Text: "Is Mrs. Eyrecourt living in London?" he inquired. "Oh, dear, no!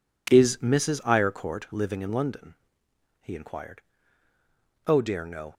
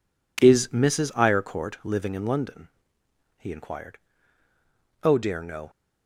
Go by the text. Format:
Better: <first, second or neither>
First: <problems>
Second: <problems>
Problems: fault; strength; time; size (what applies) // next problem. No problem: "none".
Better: neither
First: none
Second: none